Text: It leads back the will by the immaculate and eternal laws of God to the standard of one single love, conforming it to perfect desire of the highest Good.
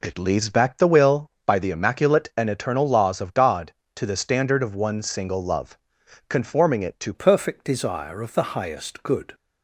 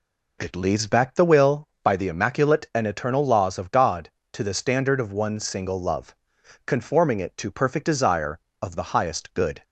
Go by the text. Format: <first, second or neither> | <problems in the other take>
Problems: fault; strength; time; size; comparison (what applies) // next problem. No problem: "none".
second | changes voice at "perfect"; from 7.1 s on; 2.2 s long